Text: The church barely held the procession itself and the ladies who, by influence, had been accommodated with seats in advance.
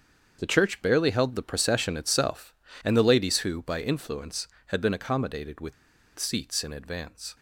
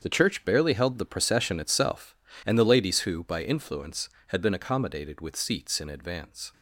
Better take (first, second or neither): second